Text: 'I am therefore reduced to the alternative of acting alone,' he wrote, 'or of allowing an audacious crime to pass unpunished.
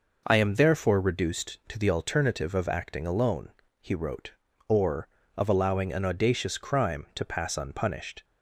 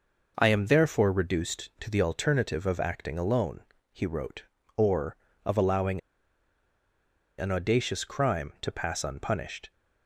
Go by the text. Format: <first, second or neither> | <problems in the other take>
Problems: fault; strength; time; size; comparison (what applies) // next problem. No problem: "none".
first | pauses between "allowing" and "an"; strong; at 6.0 s; 1.3 s long